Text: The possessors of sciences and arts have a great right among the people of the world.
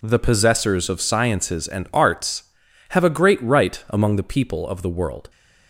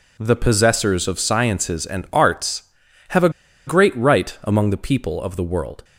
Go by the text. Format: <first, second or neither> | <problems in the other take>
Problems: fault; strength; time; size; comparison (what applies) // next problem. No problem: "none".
first | pauses between "a" and "great"; at 3.2 s; 0.37 s long